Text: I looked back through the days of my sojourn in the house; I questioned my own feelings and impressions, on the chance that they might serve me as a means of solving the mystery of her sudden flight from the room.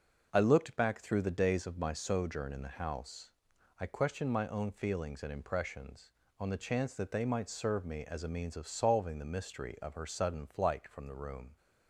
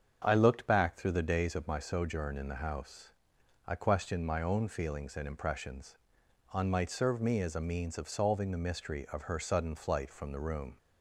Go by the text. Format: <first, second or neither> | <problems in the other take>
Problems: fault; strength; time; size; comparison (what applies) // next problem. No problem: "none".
first | starts louder than the rest; strong; until 1.2 s; 7 dB // skips "the chance that they"; at 6.7 s